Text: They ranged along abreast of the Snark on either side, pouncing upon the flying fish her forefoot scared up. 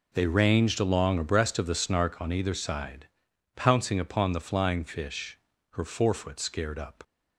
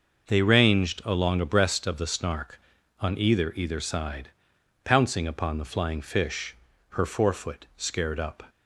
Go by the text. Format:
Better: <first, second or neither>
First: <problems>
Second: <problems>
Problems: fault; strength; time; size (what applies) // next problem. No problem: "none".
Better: first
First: pauses between "fish" and "her"; at 5.3 s; 0.38 s long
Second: says "either" twice; at 3.5 s // pauses between "fish" and "her"; slight; at 6.5 s; 0.34 s long